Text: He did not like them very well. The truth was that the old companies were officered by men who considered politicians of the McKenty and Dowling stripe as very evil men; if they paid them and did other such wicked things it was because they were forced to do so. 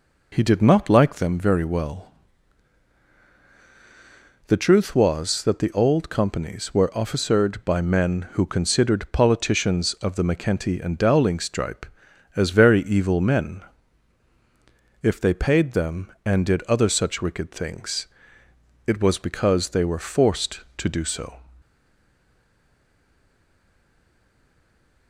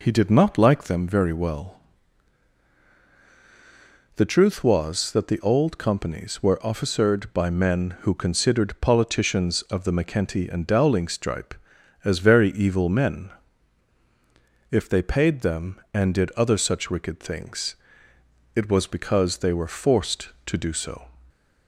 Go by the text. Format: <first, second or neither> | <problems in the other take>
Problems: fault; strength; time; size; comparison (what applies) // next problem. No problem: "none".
second | pauses between "things" and "it"; noticeable; at 18.0 s; 0.80 s long; noticeable in the second // stays silent after the last word; strong; from 21.6 s on; 3.4 s long